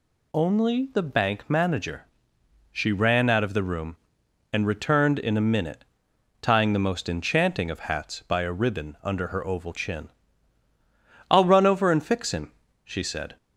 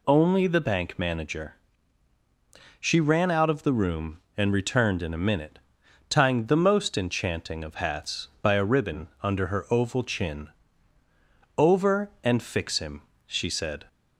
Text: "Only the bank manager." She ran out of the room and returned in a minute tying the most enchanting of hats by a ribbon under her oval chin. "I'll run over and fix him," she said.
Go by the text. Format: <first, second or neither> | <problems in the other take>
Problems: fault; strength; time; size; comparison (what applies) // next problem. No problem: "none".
first | pauses between "minute" and "tying"; noticeable; at 5.5 s; 0.52 s long; noticeable in the first // skips "I'll run"; at 11.0 s